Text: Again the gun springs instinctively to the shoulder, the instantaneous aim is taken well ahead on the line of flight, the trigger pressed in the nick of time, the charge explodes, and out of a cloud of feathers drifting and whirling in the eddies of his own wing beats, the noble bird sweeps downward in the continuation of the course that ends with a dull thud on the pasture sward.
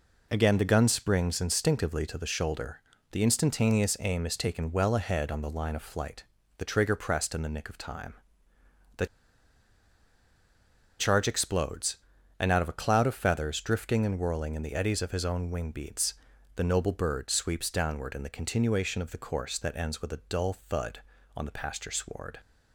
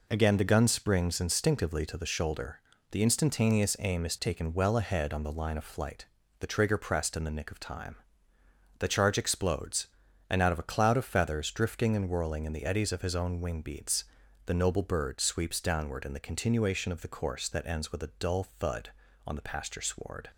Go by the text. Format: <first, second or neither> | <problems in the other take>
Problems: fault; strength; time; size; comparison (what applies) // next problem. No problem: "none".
second | pauses between "the" and "charge"; strong; at 9.0 s; 1.9 s long